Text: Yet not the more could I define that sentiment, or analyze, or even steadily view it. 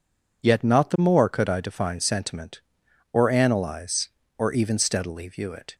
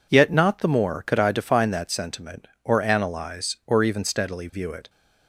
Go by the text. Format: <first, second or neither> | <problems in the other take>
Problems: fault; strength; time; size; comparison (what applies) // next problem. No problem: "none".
second | skips "that"; at 1.9 s